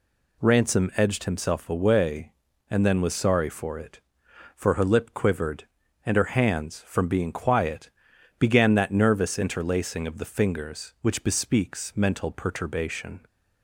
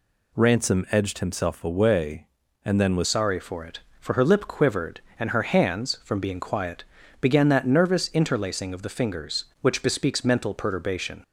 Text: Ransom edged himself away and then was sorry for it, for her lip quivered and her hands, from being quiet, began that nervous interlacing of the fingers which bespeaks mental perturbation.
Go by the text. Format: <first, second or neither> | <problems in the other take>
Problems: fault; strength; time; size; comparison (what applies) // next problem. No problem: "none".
first | changes voice at "sorry"; from 3.0 s on; 8.2 s long